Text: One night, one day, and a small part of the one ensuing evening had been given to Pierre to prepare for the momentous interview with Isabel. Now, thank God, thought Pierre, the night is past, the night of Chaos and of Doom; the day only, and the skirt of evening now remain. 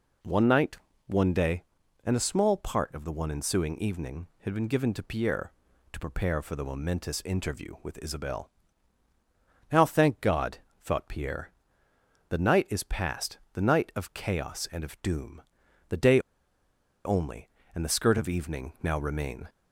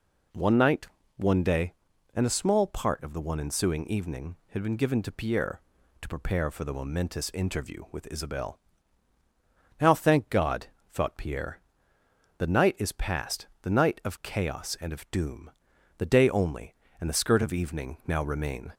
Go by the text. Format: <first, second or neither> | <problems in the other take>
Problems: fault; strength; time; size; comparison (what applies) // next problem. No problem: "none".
second | pauses between "day" and "only"; noticeable; at 16.1 s; 0.86 s long